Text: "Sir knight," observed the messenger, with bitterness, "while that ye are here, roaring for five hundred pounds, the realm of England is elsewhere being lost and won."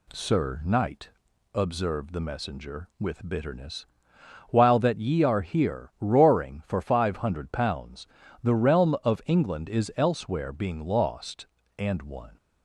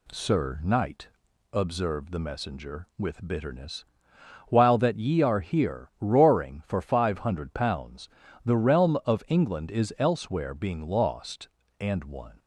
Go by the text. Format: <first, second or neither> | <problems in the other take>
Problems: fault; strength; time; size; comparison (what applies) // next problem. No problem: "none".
neither | none